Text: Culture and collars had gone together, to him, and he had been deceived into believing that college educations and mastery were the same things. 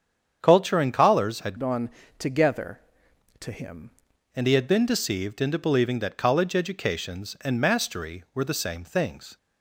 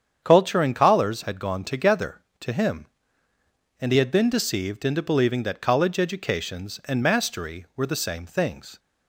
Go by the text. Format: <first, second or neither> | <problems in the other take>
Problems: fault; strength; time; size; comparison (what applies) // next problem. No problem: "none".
second | starts louder than the rest; strong; until 1.4 s; 8 dB; strong in the second // changes voice from "gone" to "him"; from 1.5 to 3.9 s; 2.4 s long // pauses between "gone" and "together"; slight; at 1.8 s; 0.30 s long